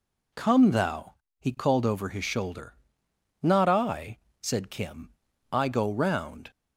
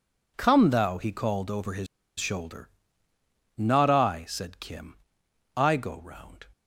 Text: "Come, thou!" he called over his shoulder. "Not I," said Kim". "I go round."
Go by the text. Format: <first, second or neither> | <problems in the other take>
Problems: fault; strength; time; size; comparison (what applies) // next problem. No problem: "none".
first | pauses between "his" and "shoulder"; slight; at 1.8 s; 0.31 s long